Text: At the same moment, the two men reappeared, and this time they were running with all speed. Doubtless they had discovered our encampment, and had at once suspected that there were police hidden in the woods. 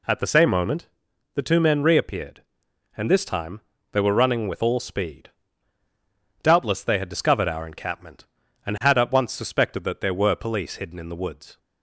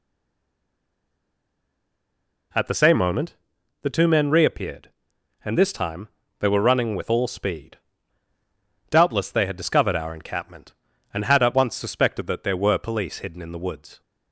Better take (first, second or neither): first